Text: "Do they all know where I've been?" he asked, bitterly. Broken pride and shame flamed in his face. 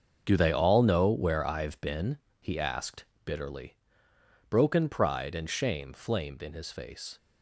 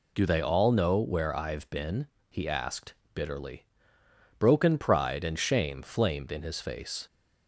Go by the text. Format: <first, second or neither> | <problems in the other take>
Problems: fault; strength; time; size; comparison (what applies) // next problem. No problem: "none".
second | gets quieter; strong; throughout; 11 dB